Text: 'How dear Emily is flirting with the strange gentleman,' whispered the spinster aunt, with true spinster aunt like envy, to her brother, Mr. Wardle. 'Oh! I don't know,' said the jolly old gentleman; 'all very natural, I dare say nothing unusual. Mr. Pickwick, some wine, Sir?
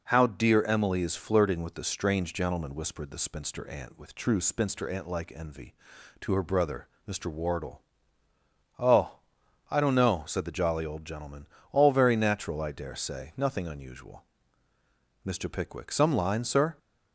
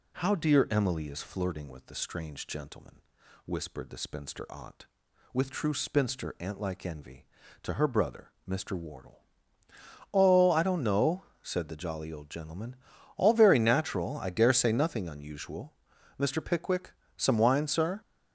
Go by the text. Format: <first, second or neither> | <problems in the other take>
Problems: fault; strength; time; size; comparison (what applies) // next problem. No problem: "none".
second | says "line" for "wine"; at 16.1 s